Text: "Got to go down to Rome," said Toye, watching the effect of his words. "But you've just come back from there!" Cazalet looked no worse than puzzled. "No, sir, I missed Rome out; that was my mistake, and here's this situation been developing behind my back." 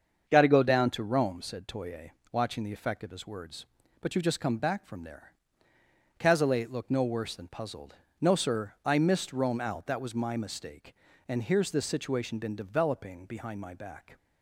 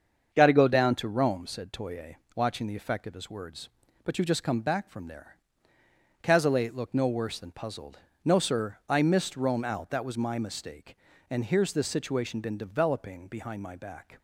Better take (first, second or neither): neither